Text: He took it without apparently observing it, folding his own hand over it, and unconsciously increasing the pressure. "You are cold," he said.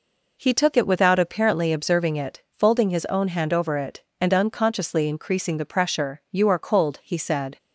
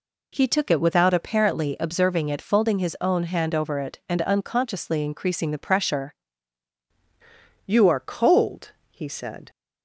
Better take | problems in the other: first | changes voice at "You"; from 7.6 s on; 1.8 s long

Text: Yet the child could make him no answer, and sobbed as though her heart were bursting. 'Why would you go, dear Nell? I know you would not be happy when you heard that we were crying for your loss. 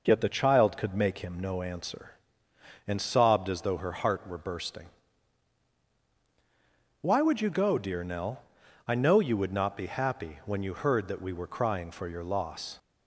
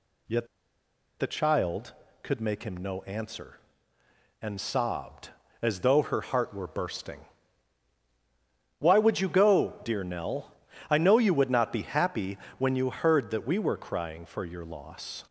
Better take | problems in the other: first | pauses between "Yet" and "the"; noticeable; at 0.4 s; 0.73 s long // pauses between "happy" and "when"; slight; at 12.3 s; 0.20 s long

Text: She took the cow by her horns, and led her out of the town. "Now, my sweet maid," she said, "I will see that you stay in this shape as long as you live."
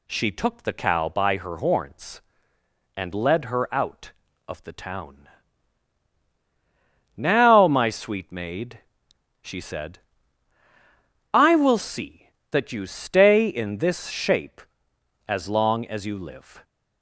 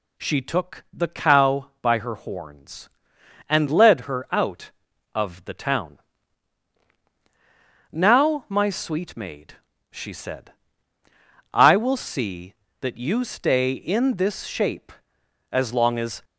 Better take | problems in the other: first | stops before "you live"; at 16.2 s

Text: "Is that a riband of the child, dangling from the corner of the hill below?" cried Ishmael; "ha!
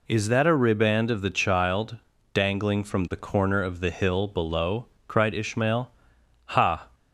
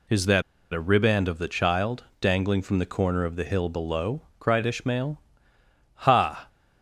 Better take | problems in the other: first | pauses between "that" and "a"; slight; at 0.4 s; 0.31 s long

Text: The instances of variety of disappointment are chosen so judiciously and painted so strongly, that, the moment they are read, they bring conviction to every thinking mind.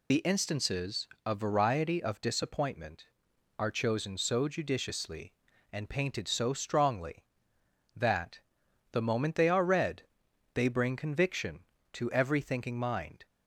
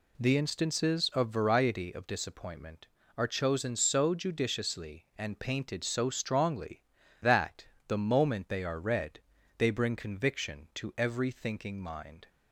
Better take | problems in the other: second | loses the start of "The"; at 0.1 s; 30 ms

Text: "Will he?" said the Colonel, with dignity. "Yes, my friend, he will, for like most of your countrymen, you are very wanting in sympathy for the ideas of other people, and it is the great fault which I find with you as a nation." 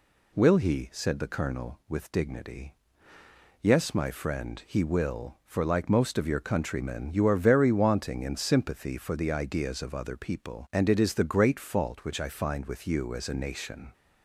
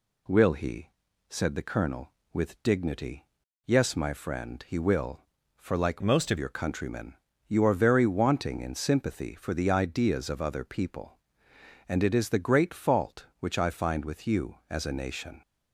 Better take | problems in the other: first | changes voice from "most" to "of"; from 6.0 to 6.3 s; 0.3 s long

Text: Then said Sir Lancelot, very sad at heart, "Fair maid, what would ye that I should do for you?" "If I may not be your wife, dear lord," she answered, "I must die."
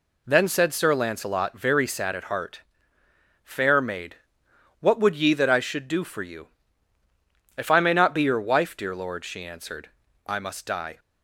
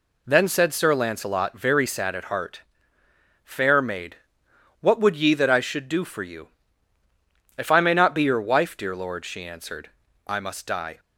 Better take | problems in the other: neither | none

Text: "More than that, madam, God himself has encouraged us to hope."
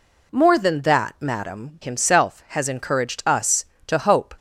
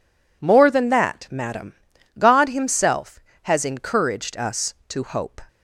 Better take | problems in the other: second | skips "God"; at 1.7 s

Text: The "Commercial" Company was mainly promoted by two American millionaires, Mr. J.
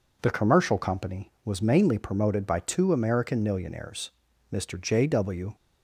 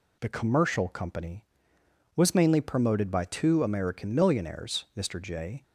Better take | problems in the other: second | goes on to say "W"; slight; from 5.0 s on; 0.48 s long

